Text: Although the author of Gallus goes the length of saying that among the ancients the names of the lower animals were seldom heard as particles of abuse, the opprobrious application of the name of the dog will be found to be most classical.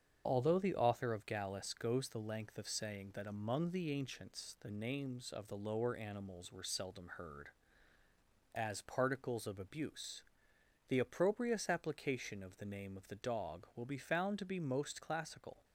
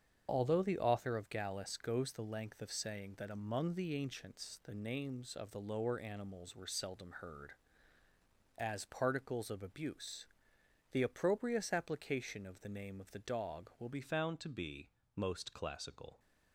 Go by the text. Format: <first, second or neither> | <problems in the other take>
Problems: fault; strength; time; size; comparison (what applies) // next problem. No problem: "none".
first | starts louder than the rest; strong; until 1.3 s; 7.5 dB; strong in the first // changes voice at "found"; from 14.0 s on; 2.1 s long // pauses between "be" and "most"; slight; at 14.9 s; 0.24 s long